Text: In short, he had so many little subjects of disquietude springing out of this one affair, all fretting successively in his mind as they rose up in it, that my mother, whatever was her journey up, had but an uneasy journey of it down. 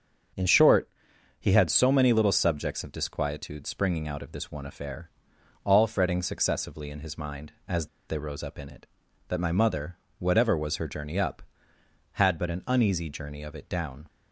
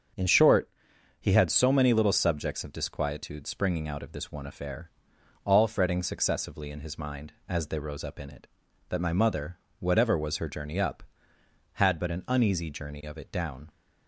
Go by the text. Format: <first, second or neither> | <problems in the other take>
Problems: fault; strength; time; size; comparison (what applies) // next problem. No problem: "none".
second | starts louder than the rest; until 1.8 s; 7 dB; also in the second // pauses between "as" and "they"; slight; at 7.8 s; 0.21 s long